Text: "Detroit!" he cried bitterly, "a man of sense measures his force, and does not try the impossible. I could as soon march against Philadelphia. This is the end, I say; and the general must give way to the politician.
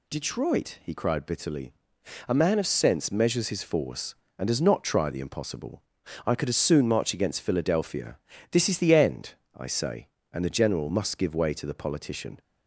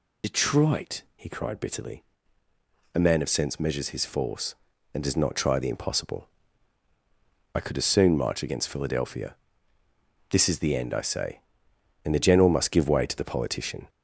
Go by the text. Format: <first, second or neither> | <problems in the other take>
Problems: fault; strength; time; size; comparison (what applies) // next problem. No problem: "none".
first | loses the start of "Detroit"; at 0.2 s; 75 ms